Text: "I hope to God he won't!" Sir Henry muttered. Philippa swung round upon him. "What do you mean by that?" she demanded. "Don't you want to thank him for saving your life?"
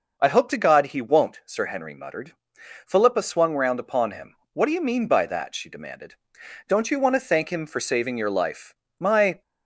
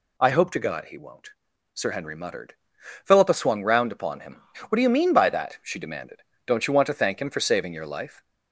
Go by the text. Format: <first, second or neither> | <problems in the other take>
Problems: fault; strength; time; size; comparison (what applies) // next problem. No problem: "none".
second | goes on to say "My"; slight; from 8.9 s on; 0.44 s long